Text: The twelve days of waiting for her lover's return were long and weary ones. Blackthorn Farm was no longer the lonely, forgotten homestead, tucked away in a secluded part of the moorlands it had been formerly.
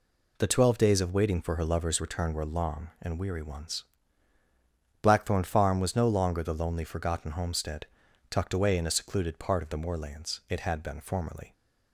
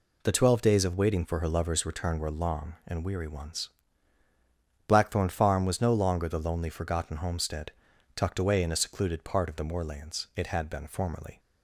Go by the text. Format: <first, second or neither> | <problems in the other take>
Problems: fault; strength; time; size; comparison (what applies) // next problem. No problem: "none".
neither | none